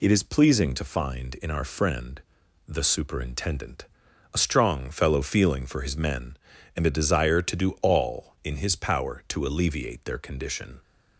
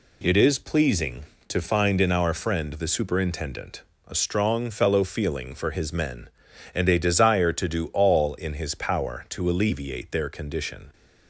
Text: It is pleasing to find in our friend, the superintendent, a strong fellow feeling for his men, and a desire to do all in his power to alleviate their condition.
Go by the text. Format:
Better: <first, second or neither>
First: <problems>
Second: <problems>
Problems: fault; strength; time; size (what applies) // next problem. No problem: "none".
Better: neither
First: none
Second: none